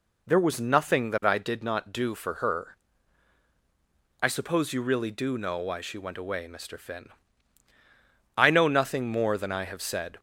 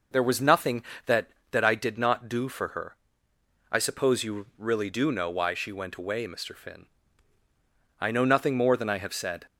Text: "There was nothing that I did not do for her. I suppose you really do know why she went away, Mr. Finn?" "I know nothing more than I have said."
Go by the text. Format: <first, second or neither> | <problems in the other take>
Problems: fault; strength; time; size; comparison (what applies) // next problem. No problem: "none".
first | says "that" twice; at 1.5 s